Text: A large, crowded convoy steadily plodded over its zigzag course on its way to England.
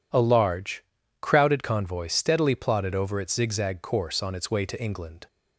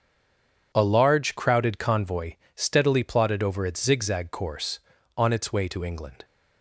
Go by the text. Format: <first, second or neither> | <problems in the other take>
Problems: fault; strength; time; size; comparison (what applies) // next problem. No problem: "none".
first | stays silent before the first word; slight; until 0.7 s; 0.7 s long // pauses between "convoy" and "steadily"; slight; at 2.3 s; 0.20 s long